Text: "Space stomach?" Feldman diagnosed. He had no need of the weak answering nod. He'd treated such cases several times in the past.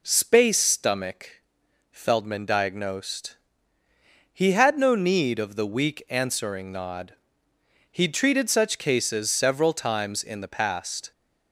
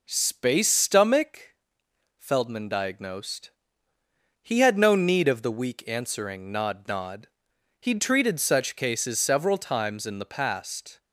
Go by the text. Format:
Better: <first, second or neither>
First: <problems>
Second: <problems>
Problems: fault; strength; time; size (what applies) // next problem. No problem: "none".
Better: first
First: none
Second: says "nod" twice; at 6.8 s